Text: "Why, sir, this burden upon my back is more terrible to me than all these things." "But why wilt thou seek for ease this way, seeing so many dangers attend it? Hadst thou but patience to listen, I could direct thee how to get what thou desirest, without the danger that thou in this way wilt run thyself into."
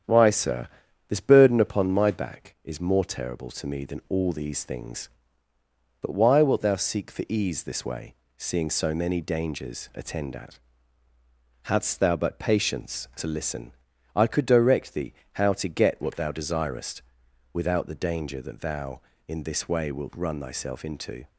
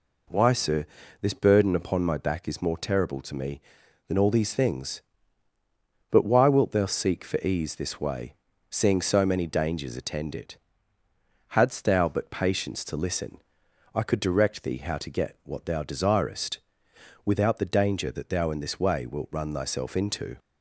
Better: second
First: starts louder than the rest; strong; until 1.4 s; 8.5 dB // says "at" for "it"; at 10.3 s // pauses between "thee" and "how"; slight; at 15.1 s; 0.20 s long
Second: none

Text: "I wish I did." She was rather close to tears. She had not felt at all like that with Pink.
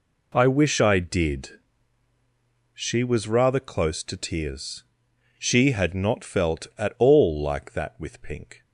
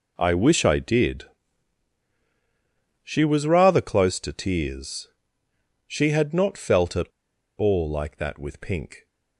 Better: first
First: none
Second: pauses between "at" and "all"; noticeable; at 7.0 s; 0.49 s long

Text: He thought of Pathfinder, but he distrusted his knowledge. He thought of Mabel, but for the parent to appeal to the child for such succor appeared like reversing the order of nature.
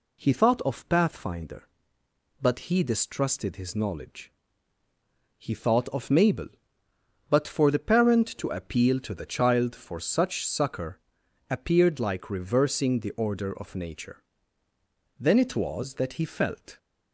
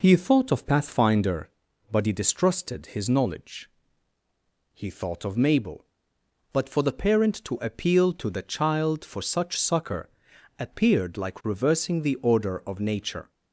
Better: second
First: pauses between "succor" and "appeared"; noticeable; at 10.9 s; 0.54 s long // goes on to say "Then it was that he felt"; from 15.1 s on; 1.5 s long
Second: pauses between "succor" and "appeared"; noticeable; at 10.0 s; 0.48 s long

